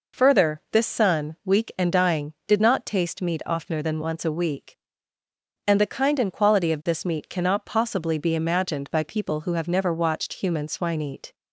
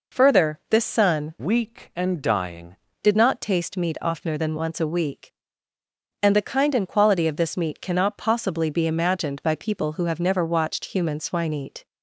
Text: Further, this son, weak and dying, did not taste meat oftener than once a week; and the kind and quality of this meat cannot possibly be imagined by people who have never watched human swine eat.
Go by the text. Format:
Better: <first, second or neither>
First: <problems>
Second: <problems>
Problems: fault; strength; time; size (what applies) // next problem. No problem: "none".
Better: first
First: none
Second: changes voice from "weak" to "dying"; from 1.4 to 2.7 s; 1.3 s long